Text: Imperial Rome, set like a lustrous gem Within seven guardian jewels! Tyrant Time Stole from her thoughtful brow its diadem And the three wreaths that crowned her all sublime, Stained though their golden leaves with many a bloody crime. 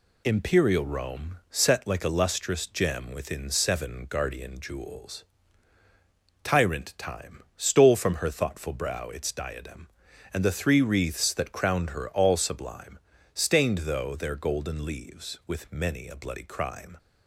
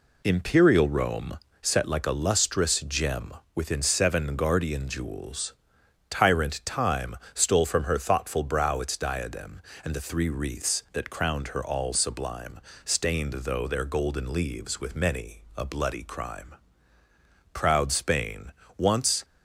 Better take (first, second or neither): first